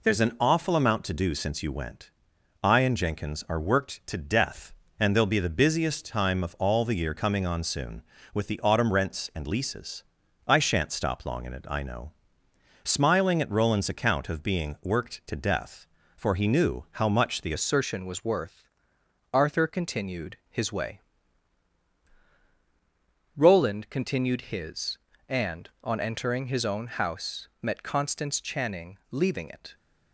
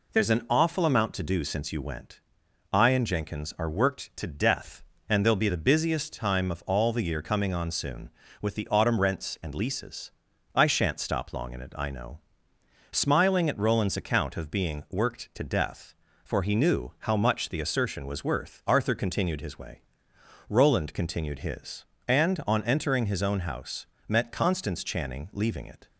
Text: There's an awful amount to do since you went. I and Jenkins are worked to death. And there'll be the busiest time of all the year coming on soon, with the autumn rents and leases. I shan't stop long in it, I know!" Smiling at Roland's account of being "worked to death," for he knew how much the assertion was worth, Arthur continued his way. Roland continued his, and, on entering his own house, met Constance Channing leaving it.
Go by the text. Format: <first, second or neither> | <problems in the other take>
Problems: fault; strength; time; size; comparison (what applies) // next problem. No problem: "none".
second | changes voice at "assertion"; from 17.5 s on; 12.2 s long